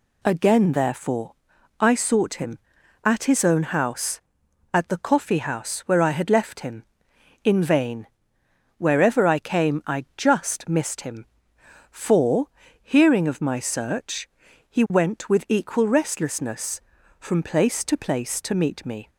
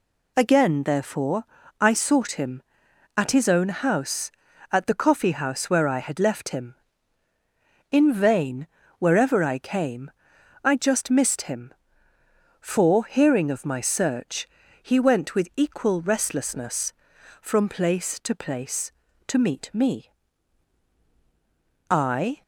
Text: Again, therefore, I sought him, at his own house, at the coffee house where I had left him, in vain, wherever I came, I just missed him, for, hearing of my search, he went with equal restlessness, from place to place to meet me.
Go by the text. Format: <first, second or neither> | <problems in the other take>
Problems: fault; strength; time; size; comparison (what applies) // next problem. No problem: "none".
first | goes on to say "I"; from 21.8 s on; 0.52 s long